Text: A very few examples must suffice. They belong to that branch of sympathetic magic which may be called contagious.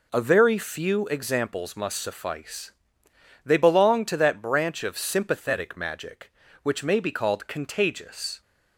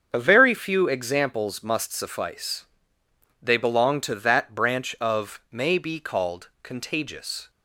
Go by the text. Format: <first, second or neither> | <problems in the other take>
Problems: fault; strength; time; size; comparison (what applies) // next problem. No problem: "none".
first | starts louder than the rest; until 1.1 s; 7 dB // skips "sympathetic magic which"; at 5.4 s // pauses between "called" and "contagious"; slight; at 6.4 s; 0.16 s long